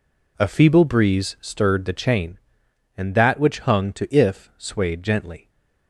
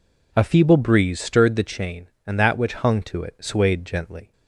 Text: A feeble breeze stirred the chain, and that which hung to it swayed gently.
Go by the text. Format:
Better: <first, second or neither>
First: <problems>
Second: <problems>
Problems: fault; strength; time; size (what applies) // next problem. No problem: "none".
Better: second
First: says "if" for "it"; at 4.1 s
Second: none